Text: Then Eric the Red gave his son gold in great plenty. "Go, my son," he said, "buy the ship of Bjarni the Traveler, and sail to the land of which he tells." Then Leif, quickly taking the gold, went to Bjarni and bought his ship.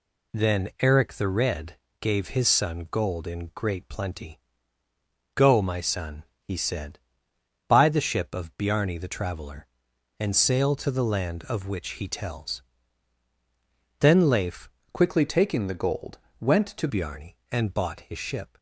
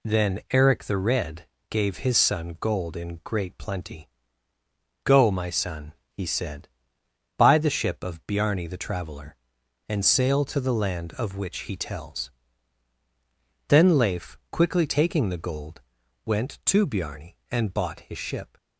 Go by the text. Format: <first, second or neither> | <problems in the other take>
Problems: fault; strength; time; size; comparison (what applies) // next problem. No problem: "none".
second | pauses between "Red" and "gave"; slight; at 1.7 s; 0.24 s long; slight in the second // changes voice from "quickly" to "to"; from 14.9 to 16.8 s; 1.9 s long